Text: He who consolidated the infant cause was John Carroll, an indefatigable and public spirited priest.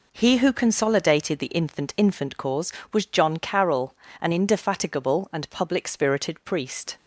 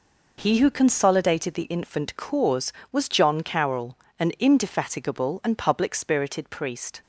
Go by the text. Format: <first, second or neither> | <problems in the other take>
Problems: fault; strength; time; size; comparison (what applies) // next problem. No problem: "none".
second | says "infant" twice; at 1.9 s